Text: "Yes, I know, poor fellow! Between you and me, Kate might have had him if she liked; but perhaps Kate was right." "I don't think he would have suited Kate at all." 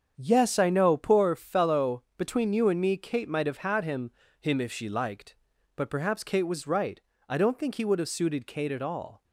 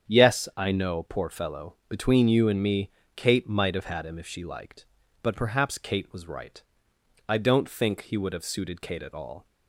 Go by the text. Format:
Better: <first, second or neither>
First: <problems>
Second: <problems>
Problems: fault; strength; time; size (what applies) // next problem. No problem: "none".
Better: second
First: starts louder than the rest; strong; until 1.1 s; 7.5 dB // says "him" twice; at 4.3 s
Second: starts louder than the rest; strong; until 1.1 s; 8 dB